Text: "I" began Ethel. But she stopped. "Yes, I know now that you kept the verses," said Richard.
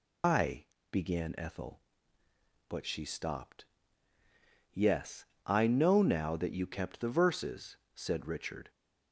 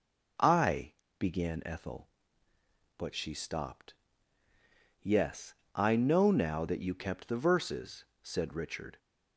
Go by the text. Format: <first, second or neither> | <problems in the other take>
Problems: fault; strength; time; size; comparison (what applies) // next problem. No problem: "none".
second | loses the start of "I"; at 0.2 s; 130 ms // pauses between "I" and "began"; slight; at 0.6 s; 0.26 s long; slight in the second